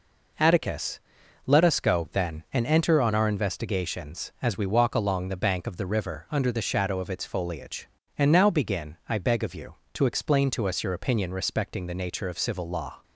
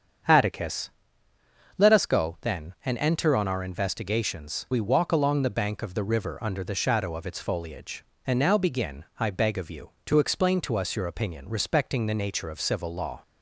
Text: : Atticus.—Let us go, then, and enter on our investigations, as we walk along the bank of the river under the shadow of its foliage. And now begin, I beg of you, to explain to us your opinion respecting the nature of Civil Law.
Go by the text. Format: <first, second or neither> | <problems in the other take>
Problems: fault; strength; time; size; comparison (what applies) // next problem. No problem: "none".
first | starts louder than the rest; strong; until 2.1 s; 7.5 dB // skips "as"; at 4.6 s